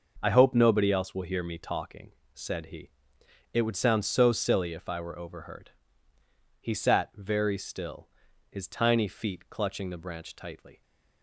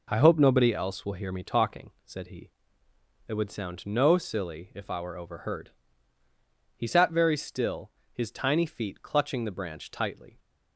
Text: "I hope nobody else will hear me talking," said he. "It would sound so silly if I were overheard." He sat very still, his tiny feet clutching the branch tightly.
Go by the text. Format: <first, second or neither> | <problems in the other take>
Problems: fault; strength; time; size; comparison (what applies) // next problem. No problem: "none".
first | says "no" for "so"; at 3.8 s